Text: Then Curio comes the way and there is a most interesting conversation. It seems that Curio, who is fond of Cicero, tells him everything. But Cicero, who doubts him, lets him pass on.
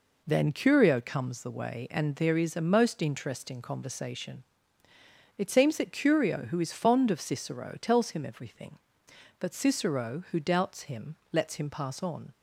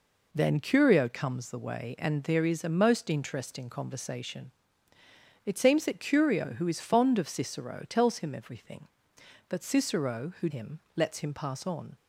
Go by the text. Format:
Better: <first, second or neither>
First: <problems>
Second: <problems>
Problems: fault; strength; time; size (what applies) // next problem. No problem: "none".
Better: first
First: none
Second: skips "doubts"; at 10.4 s